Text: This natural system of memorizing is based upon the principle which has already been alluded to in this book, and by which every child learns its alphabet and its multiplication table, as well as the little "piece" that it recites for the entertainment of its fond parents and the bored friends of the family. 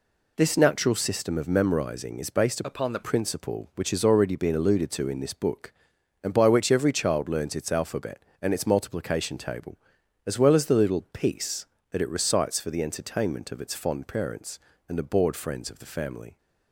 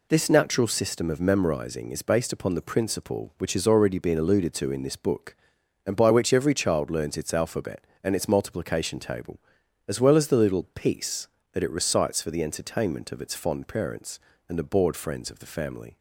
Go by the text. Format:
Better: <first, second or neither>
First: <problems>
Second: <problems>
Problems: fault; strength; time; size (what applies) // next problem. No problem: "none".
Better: second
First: changes voice from "upon" to "the"; from 2.6 to 3.0 s; 0.4 s long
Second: none